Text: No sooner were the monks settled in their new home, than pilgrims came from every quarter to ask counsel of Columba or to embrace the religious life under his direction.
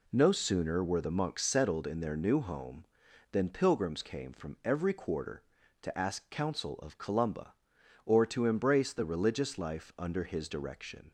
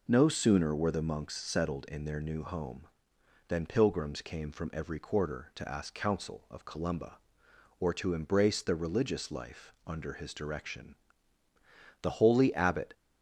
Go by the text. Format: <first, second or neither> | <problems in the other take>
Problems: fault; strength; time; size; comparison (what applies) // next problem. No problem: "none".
first | goes on to say "The holy abbot"; noticeable; from 12.0 s on; 0.90 s long